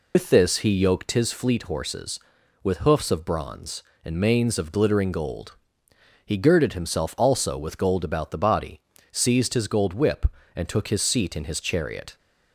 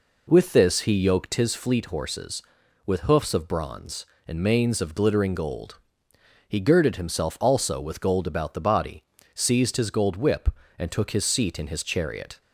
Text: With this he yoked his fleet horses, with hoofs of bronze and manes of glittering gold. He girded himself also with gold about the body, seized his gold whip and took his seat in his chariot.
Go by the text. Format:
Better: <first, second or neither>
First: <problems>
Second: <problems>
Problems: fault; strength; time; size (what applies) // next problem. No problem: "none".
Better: second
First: loses the start of "With"; at 0.1 s; 105 ms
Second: none